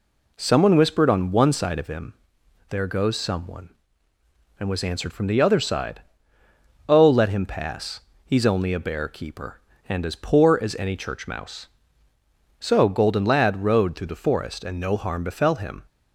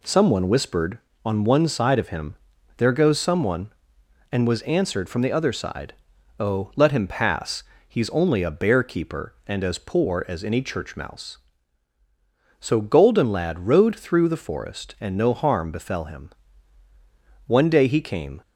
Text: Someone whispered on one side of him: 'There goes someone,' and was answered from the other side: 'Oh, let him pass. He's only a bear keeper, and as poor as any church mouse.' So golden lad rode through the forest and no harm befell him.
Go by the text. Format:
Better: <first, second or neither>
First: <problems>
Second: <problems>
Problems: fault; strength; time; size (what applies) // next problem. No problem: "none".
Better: first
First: none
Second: goes on to say "One day he came"; noticeable; from 17.4 s on; 0.94 s long